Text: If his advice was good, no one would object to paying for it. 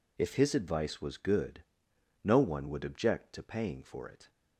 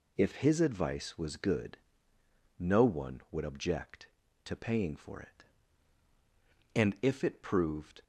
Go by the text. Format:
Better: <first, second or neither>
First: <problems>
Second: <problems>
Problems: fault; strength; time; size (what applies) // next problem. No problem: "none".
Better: first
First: none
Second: goes on to say "And if it proved"; noticeable; from 6.7 s on; 1.2 s long